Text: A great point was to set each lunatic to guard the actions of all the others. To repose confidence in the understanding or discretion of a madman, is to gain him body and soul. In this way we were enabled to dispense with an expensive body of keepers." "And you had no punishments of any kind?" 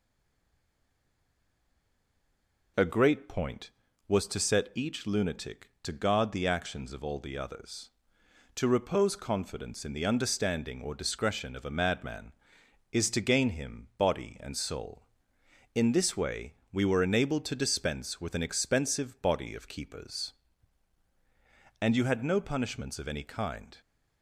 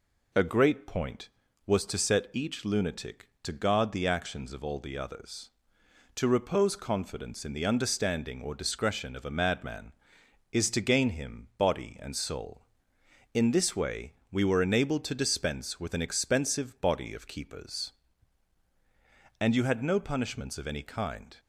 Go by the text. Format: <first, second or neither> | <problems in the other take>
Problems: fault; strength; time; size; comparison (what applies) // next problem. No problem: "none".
second | stays silent before the first word; strong; until 2.7 s; 2.7 s long // pauses between "way" and "we"; slight; at 16.5 s; 0.18 s long; slight in the second